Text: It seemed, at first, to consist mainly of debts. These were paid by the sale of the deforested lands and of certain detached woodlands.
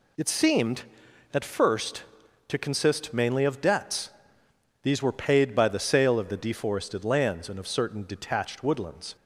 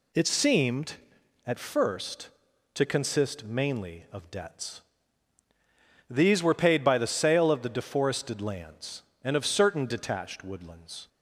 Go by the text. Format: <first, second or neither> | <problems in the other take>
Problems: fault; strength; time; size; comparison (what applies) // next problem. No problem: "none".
neither | none